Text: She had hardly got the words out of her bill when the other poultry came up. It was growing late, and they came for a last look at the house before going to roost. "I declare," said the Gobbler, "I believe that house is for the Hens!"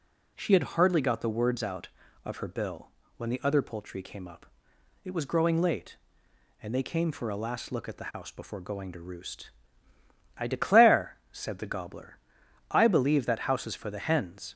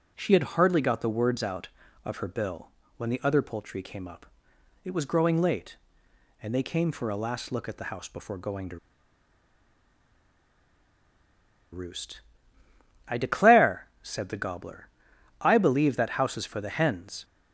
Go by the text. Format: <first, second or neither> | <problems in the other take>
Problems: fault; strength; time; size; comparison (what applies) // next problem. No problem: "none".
first | pauses between "bill" and "when"; slight; at 2.7 s; 0.26 s long; slight in the first // pauses between "to" and "roost"; strong; at 8.7 s; 2.9 s long